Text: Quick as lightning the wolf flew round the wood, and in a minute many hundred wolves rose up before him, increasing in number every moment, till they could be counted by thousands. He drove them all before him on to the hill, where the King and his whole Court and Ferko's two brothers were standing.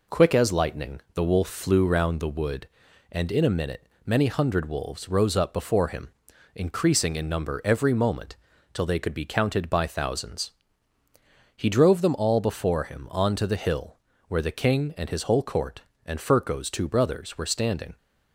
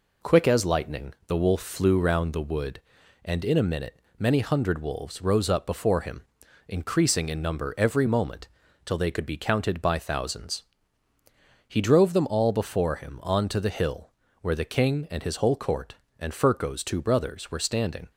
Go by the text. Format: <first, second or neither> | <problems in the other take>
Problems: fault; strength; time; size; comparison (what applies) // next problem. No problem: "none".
neither | pauses between "minute" and "many"; slight; the same in both